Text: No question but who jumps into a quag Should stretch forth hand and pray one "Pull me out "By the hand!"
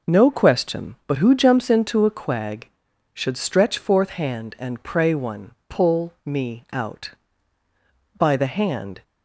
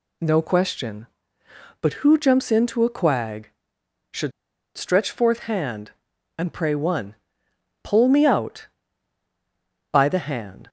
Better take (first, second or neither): first